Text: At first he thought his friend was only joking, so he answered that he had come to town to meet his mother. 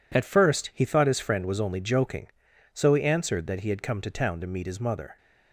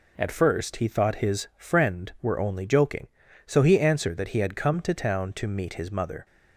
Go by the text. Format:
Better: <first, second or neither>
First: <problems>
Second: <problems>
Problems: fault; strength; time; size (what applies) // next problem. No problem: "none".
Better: first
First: none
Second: says "were" for "was"; at 2.2 s